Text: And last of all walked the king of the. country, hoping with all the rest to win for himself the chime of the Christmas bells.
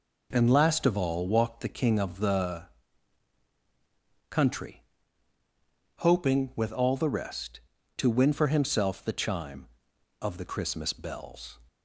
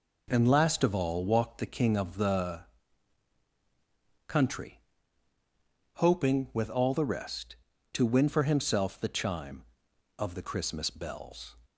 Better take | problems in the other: neither | none

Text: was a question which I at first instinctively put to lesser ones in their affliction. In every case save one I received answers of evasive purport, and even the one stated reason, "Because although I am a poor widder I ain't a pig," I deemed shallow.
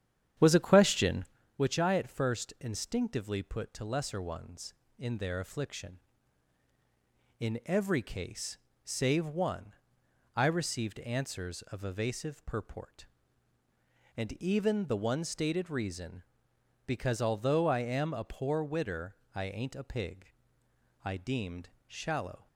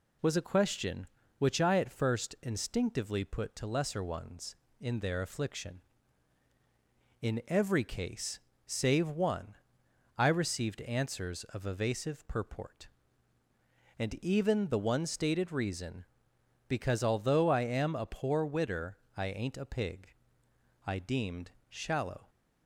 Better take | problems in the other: second | starts louder than the rest; strong; until 1.4 s; 9.5 dB // pauses between "case" and "save"; slight; at 8.5 s; 0.28 s long; slight in the second // pauses between "one" and "I"; noticeable; at 9.7 s; 0.62 s long; noticeable in the second // pauses between "widder" and "I"; slight; at 19.1 s; 0.18 s long; slight in the second // pauses between "deemed" and "shallow"; slight; at 21.6 s; 0.18 s long; slight in the second

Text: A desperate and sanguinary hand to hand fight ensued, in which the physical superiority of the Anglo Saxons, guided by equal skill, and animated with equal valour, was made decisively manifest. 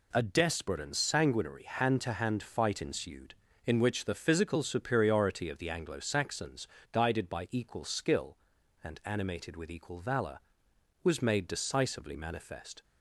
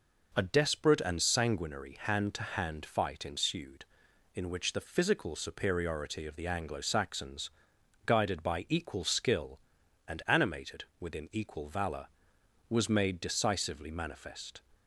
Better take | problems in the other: first | says "within" for "with"; at 10.9 s

